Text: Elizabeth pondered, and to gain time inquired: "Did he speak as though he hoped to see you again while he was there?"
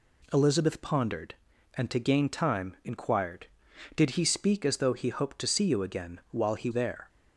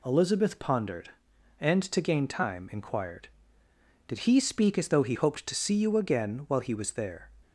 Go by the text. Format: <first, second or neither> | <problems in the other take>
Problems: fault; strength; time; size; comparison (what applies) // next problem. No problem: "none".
second | skips "was"; at 6.7 s